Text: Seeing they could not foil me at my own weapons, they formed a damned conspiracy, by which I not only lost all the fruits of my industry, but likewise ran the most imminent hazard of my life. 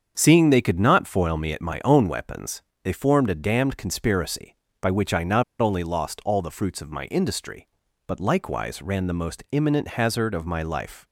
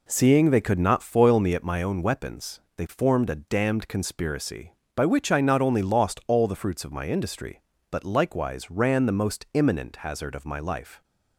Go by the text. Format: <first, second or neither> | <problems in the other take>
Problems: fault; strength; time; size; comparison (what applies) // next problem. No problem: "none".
second | starts louder than the rest; strong; until 1.1 s; 7.5 dB // pauses between "not" and "only"; slight; at 5.4 s; 0.16 s long